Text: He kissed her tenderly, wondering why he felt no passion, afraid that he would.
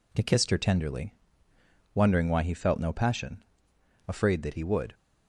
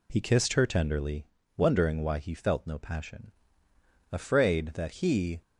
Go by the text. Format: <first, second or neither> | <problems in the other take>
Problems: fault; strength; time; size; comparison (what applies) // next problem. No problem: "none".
first | stops before "would"; at 5.4 s